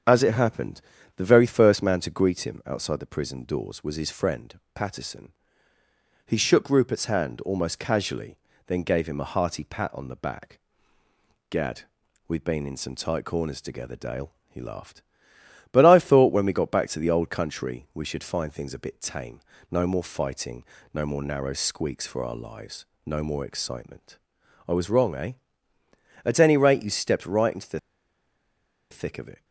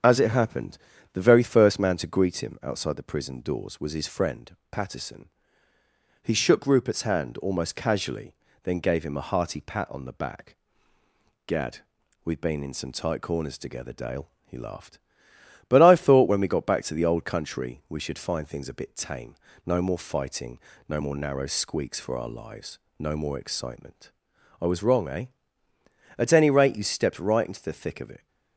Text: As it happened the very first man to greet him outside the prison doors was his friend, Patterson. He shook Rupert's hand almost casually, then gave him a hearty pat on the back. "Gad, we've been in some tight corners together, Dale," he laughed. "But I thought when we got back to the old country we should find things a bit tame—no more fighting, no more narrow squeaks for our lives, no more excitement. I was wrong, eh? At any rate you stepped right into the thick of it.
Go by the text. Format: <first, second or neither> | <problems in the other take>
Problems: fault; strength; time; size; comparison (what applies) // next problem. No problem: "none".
second | starts louder than the rest; strong; until 1.4 s; 7.5 dB; strong in the second // pauses between "happened" and "the"; slight; at 0.7 s; 0.36 s long; slight in the second // pauses between "the" and "thick"; at 27.7 s; 1.1 s long